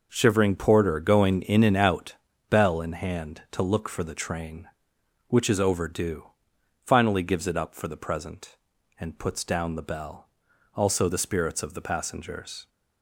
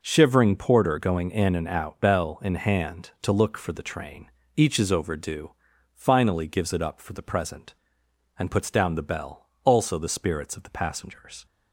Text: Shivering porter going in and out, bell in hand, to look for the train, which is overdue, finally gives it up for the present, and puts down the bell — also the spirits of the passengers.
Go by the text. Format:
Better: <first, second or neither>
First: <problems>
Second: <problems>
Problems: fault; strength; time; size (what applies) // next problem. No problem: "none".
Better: first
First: none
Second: says "each" for "which"; at 4.5 s